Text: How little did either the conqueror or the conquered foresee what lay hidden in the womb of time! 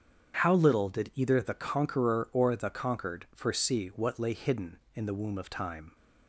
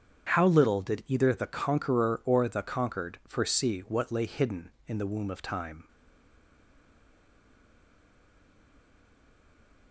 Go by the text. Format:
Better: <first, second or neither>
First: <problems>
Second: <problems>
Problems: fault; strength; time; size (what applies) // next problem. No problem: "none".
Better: first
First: starts louder than the rest; strong; until 1.4 s; 7.5 dB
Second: starts louder than the rest; strong; until 1.3 s; 7.5 dB // stays silent after the last word; strong; from 5.8 s on; 4.1 s long